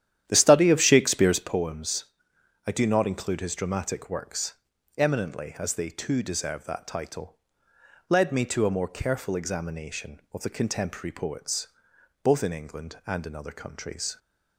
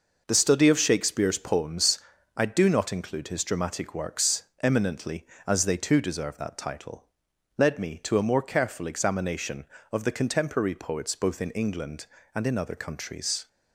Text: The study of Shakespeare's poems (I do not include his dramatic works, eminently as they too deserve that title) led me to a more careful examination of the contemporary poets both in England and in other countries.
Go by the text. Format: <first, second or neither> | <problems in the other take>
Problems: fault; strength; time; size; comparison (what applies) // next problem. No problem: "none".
second | starts louder than the rest; strong; until 1.5 s; 11 dB // pauses between "poets" and "both"; noticeable; at 11.6 s; 0.56 s long